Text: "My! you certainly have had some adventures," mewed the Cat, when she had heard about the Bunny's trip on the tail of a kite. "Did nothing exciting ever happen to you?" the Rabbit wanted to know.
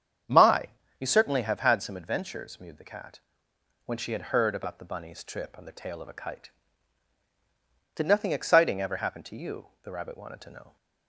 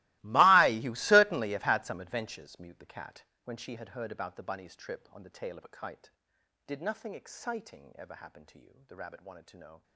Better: first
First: starts louder than the rest; strong; until 1.5 s; 8 dB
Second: gets quieter; strong; throughout; 19.5 dB // starts louder than the rest; strong; until 1.2 s; 20.5 dB

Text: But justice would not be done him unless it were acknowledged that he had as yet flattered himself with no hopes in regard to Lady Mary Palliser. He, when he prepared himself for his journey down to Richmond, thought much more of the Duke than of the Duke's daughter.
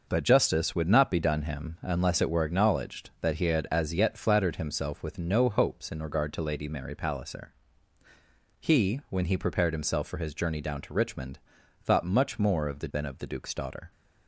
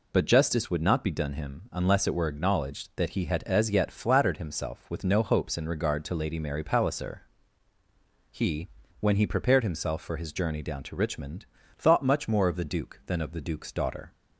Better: second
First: skips "Duke"; at 12.9 s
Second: none

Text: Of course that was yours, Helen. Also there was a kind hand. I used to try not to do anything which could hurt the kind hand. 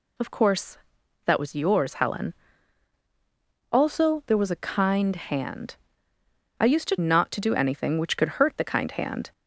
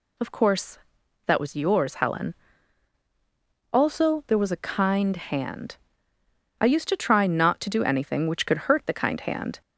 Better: second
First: skips "try"; at 6.9 s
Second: none

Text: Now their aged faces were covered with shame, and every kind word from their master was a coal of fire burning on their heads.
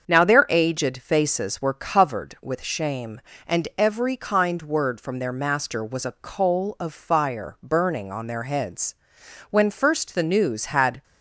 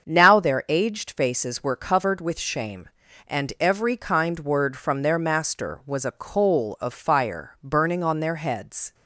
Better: second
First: starts louder than the rest; until 1.1 s; 7 dB // goes on to say "When first the news had"; from 9.5 s on; 1.5 s long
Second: starts louder than the rest; until 1.1 s; 7 dB

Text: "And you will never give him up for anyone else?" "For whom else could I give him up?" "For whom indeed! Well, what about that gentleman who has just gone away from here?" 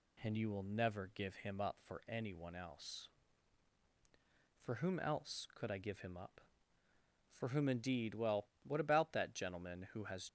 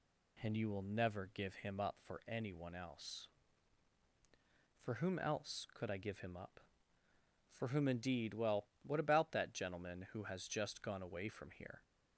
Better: second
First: stops before "just gone away from here"; at 10.2 s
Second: none

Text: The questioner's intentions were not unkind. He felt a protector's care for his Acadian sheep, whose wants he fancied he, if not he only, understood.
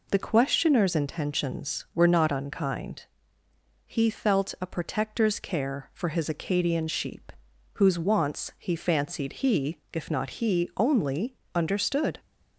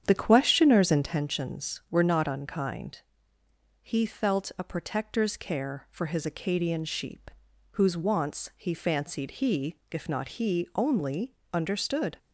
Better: first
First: none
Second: starts louder than the rest; strong; until 1.2 s; 8.5 dB

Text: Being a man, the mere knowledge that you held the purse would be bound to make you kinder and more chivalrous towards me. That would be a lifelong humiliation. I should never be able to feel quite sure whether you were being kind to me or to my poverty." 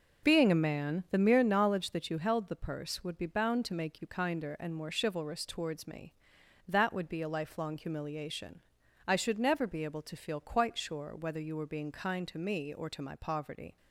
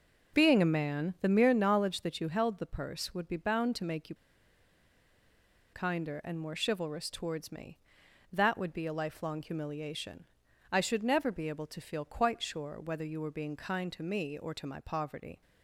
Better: first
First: none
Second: pauses between "you" and "kinder"; strong; at 4.1 s; 1.5 s long

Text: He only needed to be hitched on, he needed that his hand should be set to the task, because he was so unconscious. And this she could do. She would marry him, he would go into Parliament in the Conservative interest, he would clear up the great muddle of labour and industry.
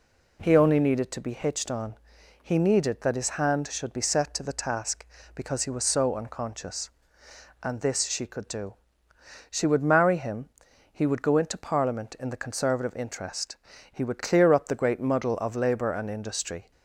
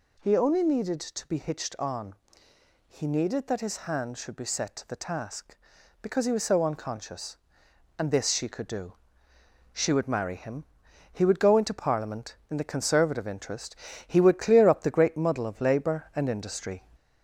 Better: first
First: none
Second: gets louder; slight; throughout; 3 dB

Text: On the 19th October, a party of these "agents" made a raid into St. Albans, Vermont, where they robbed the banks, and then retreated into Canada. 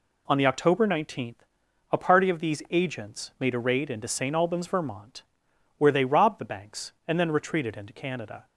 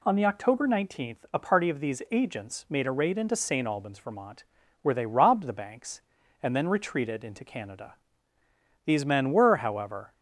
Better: first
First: none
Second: goes on to say "These men were however"; from 8.8 s on; 1.3 s long

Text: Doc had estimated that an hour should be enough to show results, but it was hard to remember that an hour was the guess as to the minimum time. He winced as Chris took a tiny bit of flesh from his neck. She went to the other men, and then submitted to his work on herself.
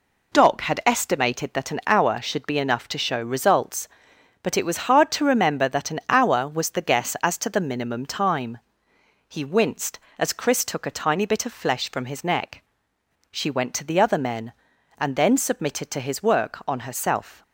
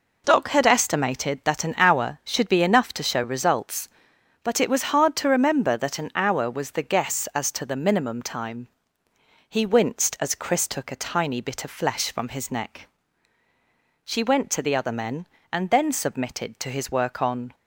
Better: first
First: none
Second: stops before "herself"; at 17.5 s

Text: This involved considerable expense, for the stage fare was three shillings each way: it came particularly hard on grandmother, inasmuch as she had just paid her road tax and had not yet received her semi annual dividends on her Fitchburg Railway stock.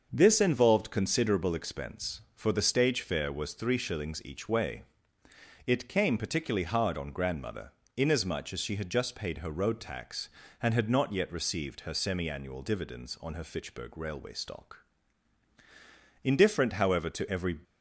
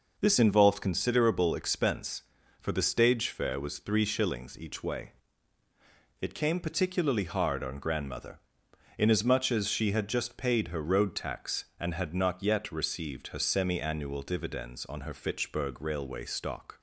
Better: second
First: starts louder than the rest; until 1.1 s; 6.5 dB // goes on to say "Indifferent however to every"; from 16.2 s on; 1.3 s long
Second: none

